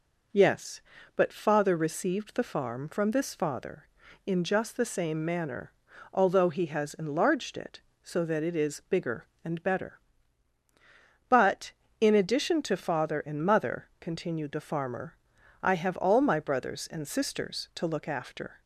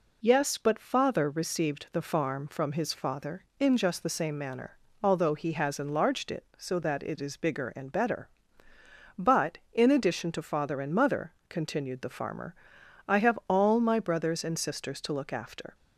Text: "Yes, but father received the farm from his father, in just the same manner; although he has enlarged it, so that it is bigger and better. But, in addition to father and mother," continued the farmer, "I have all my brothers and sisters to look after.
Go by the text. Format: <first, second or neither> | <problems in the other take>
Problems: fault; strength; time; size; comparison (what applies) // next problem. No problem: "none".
second | says "this" for "his"; at 3.0 s